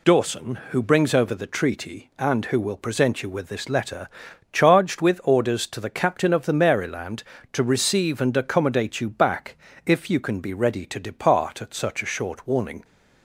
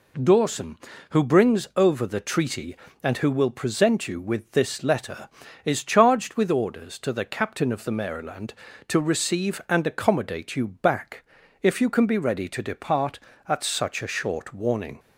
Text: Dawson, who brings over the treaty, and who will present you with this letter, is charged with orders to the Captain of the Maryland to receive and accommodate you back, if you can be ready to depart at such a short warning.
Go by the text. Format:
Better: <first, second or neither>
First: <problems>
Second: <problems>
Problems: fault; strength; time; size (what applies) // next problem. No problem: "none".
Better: second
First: skips "is"; at 4.2 s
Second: none